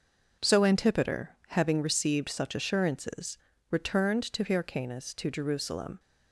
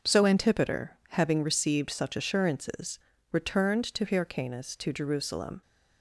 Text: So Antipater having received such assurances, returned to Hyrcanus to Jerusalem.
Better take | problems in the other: neither | none

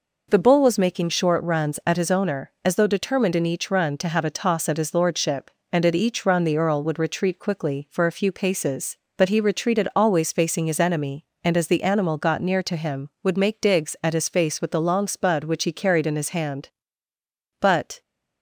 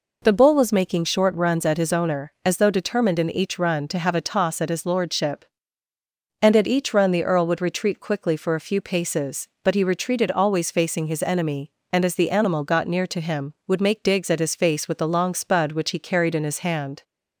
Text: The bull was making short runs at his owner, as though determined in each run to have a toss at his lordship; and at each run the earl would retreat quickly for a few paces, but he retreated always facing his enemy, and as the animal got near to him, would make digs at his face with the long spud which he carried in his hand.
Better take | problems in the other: second | goes on to say "But"; slight; from 17.5 s on; 0.42 s long

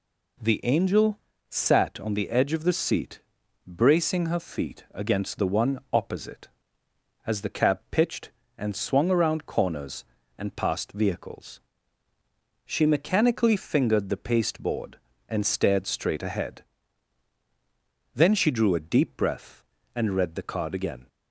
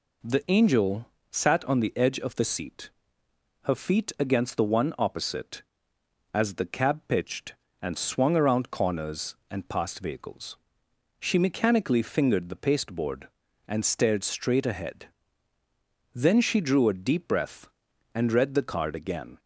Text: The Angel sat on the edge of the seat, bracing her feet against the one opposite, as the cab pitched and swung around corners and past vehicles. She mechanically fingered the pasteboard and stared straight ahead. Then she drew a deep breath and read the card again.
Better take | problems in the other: first | pauses between "Angel" and "sat"; slight; at 1.0 s; 0.24 s long; slight in the first // skips "bracing"; at 3.2 s

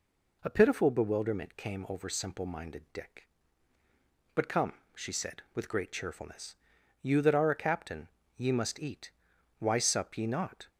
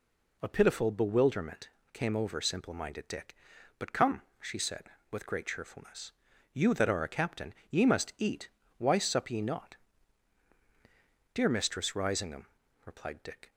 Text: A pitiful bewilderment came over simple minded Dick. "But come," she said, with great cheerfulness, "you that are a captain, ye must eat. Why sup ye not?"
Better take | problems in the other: first | pauses between "bewilderment" and "came"; slight; at 1.6 s; 0.24 s long // goes on to say "Dear Mistress Risingham replied Dick"; strong; from 11.3 s on; 2.1 s long

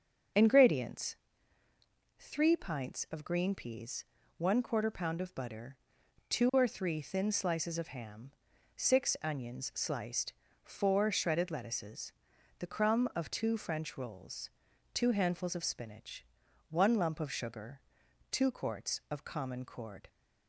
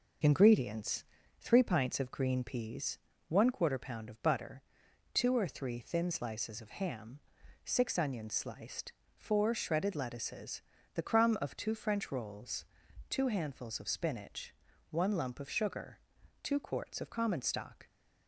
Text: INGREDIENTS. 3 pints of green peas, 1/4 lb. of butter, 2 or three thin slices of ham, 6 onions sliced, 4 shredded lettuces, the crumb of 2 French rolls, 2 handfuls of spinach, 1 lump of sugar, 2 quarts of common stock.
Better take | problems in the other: second | starts louder than the rest; until 2.4 s; 6.5 dB // says "cord" for "stock"; at 19.6 s

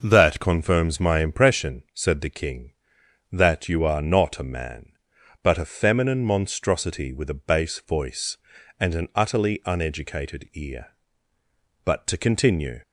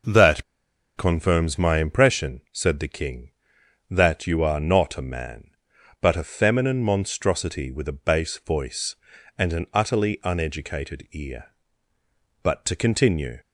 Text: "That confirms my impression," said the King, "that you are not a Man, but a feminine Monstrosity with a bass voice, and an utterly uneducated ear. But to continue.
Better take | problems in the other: first | pauses between "That" and "confirms"; noticeable; at 0.4 s; 0.53 s long

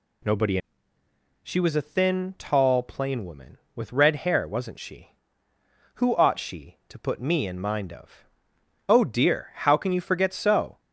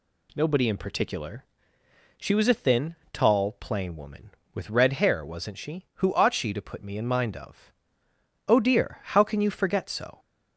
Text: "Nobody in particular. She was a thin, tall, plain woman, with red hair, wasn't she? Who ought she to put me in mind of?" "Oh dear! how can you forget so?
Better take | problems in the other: second | skips "in particular"; at 0.9 s

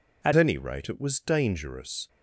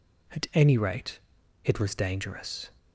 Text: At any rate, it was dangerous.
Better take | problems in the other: second | changes voice at "any"; from 0.3 s on; 1.7 s long

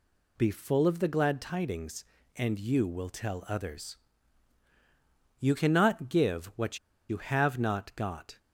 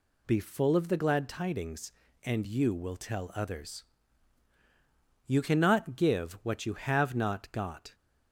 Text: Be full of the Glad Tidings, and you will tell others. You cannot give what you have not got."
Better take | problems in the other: second | pauses between "what" and "you"; slight; at 6.7 s; 0.31 s long

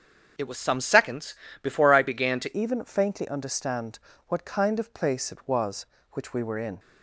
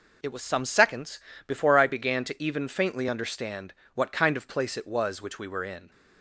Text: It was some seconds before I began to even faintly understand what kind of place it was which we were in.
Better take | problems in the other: second | starts louder than the rest; strong; until 1.6 s; 7 dB // pauses between "seconds" and "before"; slight; at 1.3 s; 0.26 s long; slight in the second // changes voice at "even"; from 2.5 s on; 4.2 s long // pauses between "understand" and "what"; slight; at 3.9 s; 0.30 s long; slight in the second

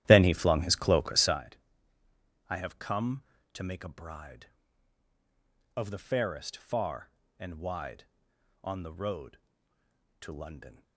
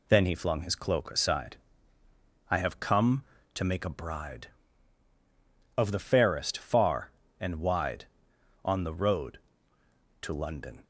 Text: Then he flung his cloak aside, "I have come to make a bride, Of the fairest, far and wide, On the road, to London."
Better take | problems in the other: second | starts louder than the rest; strong; until 1.4 s; 12.5 dB

